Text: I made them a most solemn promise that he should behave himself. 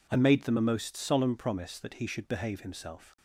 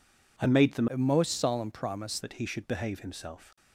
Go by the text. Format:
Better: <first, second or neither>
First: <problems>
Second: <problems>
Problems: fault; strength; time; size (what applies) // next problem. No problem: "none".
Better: first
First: none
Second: changes voice from "a" to "promise"; from 0.8 to 2.1 s; 1.3 s long